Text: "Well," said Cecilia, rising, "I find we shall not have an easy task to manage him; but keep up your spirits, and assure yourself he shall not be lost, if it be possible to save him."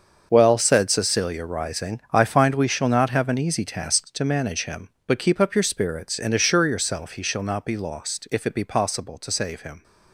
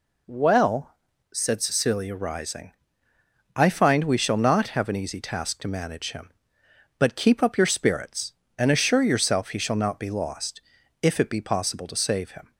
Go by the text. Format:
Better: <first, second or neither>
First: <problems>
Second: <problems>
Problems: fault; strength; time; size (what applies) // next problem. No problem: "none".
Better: second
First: gets quieter; strong; throughout; 12 dB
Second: none